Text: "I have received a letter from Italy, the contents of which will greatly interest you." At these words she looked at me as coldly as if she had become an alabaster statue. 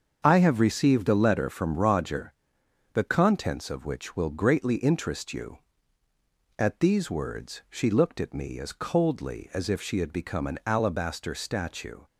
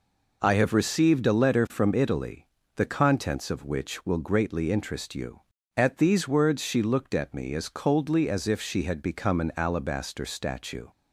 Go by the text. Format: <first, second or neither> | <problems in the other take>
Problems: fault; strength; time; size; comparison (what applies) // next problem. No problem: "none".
second | starts louder than the rest; until 1.2 s; 7 dB // says "Roger" for "Italy"; at 1.7 s